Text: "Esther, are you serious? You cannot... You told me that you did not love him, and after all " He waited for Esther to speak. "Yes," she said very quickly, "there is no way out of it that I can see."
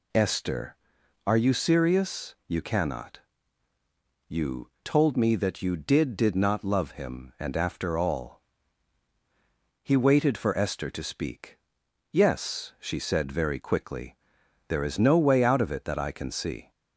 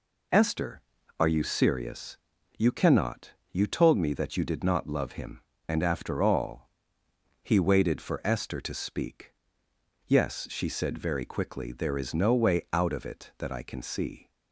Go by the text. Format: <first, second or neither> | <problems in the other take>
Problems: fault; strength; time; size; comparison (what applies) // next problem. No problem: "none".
second | says "did" twice; at 6.1 s